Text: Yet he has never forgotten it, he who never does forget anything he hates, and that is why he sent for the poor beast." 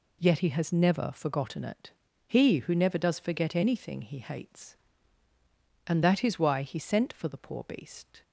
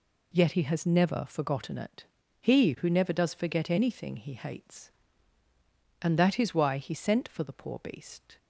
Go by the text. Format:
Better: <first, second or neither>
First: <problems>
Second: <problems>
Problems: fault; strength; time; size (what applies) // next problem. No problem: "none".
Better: neither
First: none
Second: none